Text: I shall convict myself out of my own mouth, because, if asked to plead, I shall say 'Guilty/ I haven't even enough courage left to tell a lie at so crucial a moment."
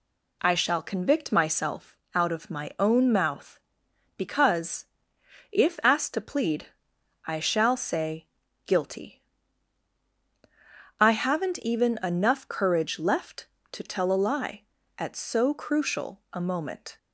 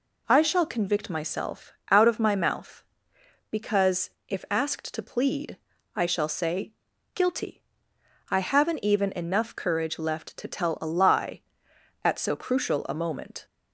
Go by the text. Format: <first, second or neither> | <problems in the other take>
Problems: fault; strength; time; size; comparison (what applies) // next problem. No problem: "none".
first | pauses between "myself" and "out"; slight; at 1.7 s; 0.18 s long; slight in the first // skips "own"; at 2.3 s // pauses between "say" and "Guilty"; at 6.7 s; 0.40 s long; also in the first